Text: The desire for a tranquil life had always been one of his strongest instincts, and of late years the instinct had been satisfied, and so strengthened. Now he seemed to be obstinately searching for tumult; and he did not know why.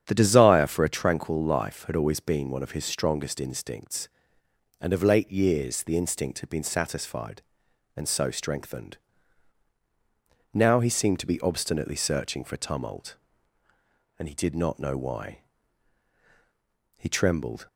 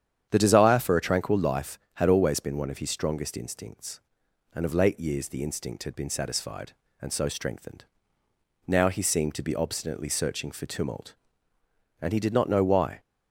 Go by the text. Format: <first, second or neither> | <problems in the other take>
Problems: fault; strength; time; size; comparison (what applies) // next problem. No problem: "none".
second | starts louder than the rest; strong; until 1.0 s; 8.5 dB; strong in the second // goes on to say "He trembled"; noticeable; from 16.9 s on; 0.68 s long